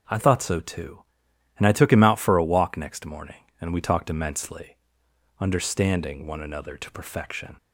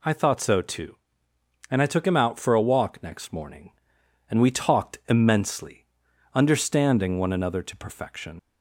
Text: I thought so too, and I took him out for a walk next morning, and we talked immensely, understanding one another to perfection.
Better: first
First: none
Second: leaves "perfection" unfinished; at 8.3 s; 65 ms

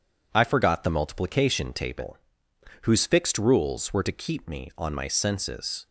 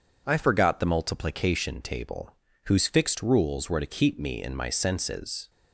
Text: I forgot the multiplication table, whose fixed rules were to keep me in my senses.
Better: second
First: says "on" for "in"; at 4.7 s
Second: none

